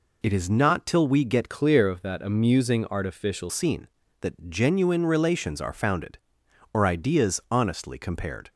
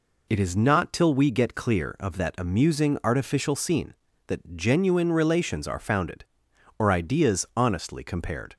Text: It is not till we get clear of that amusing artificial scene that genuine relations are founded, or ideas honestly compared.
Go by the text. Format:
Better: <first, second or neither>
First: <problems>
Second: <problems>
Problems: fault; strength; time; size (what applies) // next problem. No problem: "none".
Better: second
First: changes voice from "clear" to "artificial"; from 1.4 to 3.5 s; 2.1 s long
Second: none